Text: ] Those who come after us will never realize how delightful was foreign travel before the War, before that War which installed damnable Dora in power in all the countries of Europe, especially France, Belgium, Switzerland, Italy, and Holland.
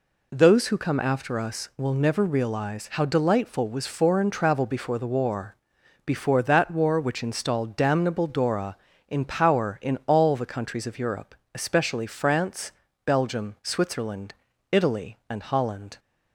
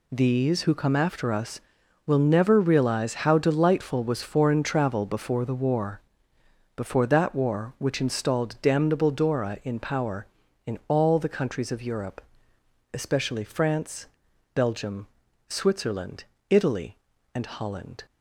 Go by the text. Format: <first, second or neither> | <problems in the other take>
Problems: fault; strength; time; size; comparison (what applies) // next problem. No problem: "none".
first | says "These" for "Those"; at 0.1 s